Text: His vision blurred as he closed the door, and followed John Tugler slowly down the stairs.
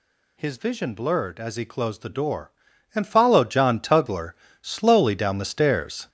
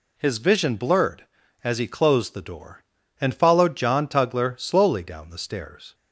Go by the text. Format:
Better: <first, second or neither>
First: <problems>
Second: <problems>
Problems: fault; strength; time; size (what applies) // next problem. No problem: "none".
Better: second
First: gets louder; throughout; 7 dB // pauses between "Tugler" and "slowly"; slight; at 4.3 s; 0.26 s long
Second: none